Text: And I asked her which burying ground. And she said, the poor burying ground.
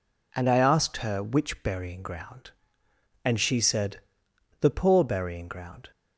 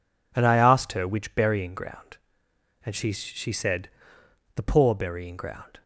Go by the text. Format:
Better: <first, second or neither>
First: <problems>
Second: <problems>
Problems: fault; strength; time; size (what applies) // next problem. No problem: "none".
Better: first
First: none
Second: says "she" twice; at 3.1 s